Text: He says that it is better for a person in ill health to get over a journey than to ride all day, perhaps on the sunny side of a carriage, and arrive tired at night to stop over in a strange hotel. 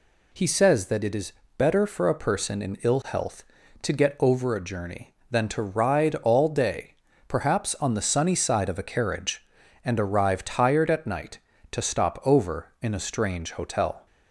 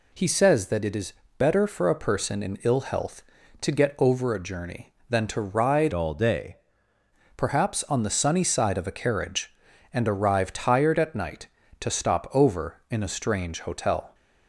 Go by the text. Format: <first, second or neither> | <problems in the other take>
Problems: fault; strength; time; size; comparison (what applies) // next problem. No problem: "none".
first | pauses between "is" and "better"; slight; at 1.1 s; 0.26 s long; slight in the first // changes voice from "all" to "day"; from 5.9 to 6.5 s; 0.6 s long